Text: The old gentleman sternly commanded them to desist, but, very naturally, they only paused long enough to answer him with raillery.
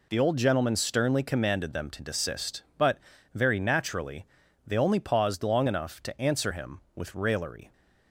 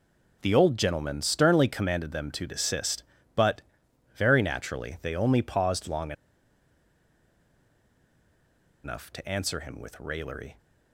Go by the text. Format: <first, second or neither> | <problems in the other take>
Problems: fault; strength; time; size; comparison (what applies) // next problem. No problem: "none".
first | pauses between "long" and "enough"; strong; at 6.1 s; 2.7 s long